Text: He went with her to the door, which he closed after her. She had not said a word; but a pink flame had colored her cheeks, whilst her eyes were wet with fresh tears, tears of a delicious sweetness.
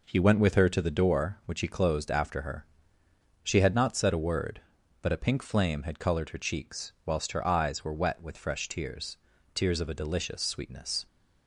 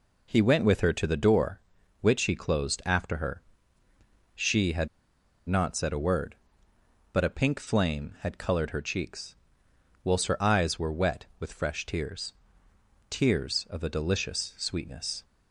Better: first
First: none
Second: pauses between "had" and "not"; noticeable; at 4.8 s; 0.61 s long

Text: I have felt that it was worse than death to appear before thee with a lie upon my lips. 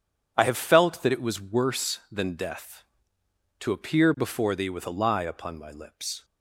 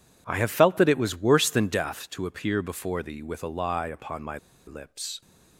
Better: first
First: none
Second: pauses between "my" and "lips"; slight; at 4.3 s; 0.29 s long

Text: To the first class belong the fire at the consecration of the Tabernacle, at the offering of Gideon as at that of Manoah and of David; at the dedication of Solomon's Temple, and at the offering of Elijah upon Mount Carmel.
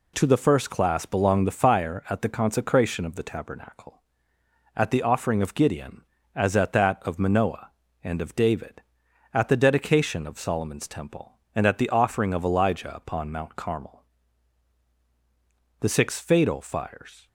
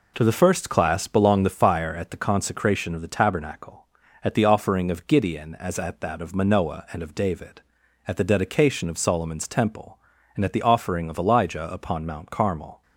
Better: second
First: goes on to say "The six fatal fires"; from 15.7 s on; 1.4 s long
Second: none

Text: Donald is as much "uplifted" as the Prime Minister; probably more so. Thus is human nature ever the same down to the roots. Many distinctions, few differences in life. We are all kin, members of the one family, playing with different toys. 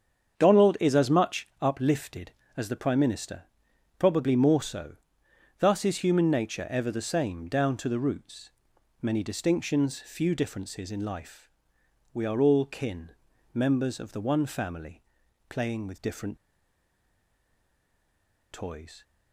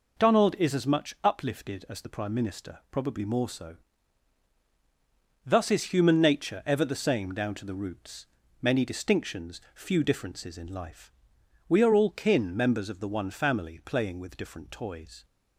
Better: second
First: starts louder than the rest; strong; until 1.4 s; 7.5 dB // pauses between "different" and "toys"; strong; at 16.3 s; 2.1 s long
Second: none

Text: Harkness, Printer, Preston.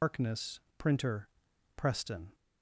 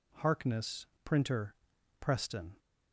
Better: second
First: loses the start of "Harkness"; at 0.0 s; 160 ms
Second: none

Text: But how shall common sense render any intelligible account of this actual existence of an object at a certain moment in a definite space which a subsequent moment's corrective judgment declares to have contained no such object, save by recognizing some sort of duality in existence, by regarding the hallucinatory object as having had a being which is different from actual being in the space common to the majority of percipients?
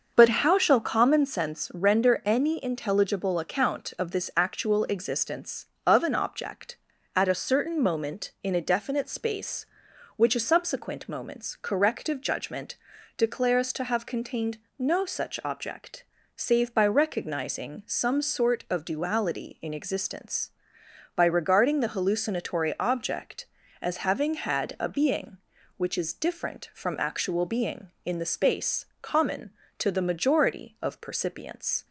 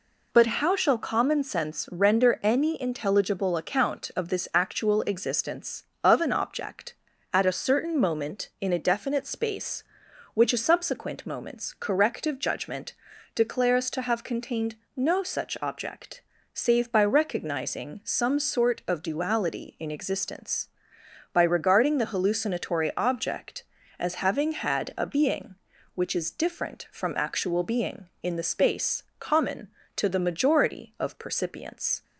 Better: second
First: starts louder than the rest; until 1.4 s; 6.5 dB // pauses between "judgment" and "declares"; at 12.7 s; 0.42 s long // pauses between "contained" and "no"; slight; at 14.5 s; 0.20 s long // pauses between "space" and "common"; slight; at 28.8 s; 0.16 s long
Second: pauses between "judgment" and "declares"; at 12.9 s; 0.42 s long // pauses between "contained" and "no"; slight; at 14.7 s; 0.20 s long // pauses between "space" and "common"; slight; at 29.0 s; 0.16 s long

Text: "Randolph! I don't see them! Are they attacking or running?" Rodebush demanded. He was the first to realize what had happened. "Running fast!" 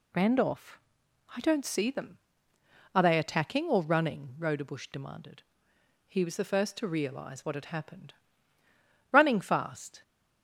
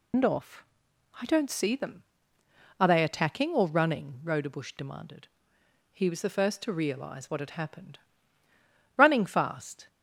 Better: first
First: none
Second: loses the start of "Randolph"; at 0.1 s; 145 ms

